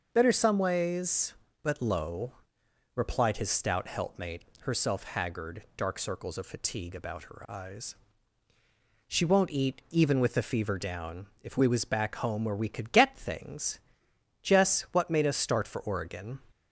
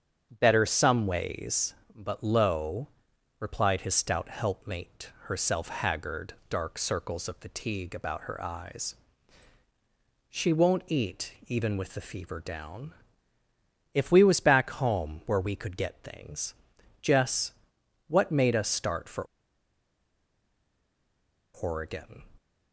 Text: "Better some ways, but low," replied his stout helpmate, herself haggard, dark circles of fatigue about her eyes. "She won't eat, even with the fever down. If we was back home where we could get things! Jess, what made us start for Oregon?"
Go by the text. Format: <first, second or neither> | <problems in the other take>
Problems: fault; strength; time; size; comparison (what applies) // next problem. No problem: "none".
first | starts louder than the rest; strong; until 1.3 s; 7.5 dB; noticeable in the first // pauses between "for" and "Oregon"; strong; at 19.2 s; 2.3 s long